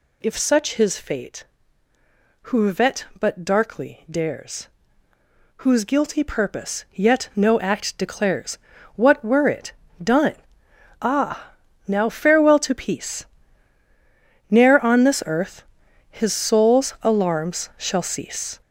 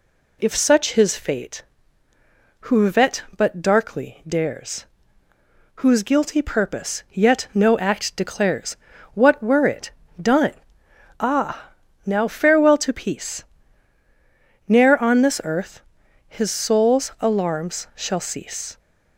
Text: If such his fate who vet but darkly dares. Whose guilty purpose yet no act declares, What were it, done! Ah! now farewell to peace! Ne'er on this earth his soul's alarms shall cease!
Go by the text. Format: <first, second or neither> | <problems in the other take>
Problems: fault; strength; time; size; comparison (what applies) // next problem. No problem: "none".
second | gets louder; throughout; 7 dB // pauses between "earth" and "his"; noticeable; at 15.6 s; 0.48 s long; noticeable in the second